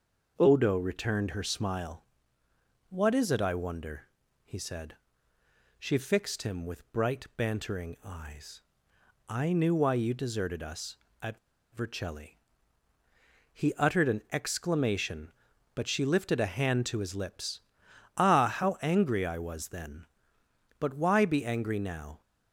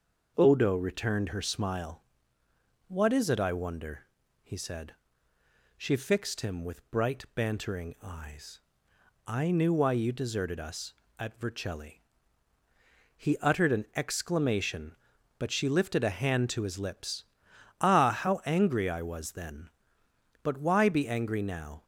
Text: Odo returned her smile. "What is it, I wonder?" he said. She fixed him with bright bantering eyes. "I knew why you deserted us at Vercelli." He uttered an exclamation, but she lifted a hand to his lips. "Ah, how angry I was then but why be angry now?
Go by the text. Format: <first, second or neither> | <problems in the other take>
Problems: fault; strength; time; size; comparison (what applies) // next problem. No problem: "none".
second | pauses between "at" and "Vercelli"; slight; at 11.3 s; 0.36 s long